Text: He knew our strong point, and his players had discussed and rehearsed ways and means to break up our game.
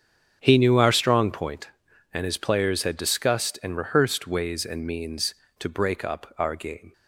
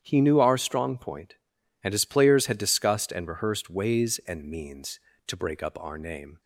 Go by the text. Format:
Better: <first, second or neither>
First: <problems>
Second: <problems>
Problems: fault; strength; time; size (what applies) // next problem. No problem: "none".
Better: first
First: starts louder than the rest; strong; until 1.4 s; 7.5 dB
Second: starts louder than the rest; strong; until 1.0 s; 9 dB // says "name" for "game"; at 5.9 s